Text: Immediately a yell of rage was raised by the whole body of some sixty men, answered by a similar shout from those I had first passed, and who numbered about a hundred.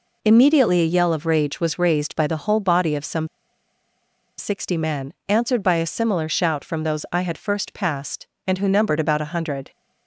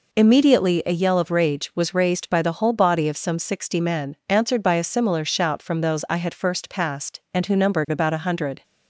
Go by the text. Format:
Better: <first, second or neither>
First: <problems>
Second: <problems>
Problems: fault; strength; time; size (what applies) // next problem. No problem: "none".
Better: second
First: pauses between "some" and "sixty"; at 3.2 s; 1.1 s long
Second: none